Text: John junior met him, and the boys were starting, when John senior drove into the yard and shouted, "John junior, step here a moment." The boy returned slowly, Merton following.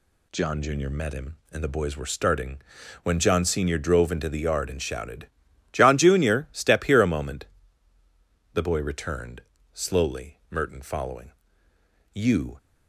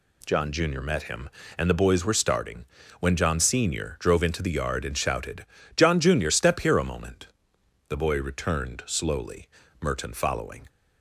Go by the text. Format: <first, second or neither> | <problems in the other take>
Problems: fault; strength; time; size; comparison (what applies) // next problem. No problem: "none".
second | pauses between "returned" and "slowly"; slight; at 9.4 s; 0.30 s long // goes on to say "You"; slight; from 12.1 s on; 0.46 s long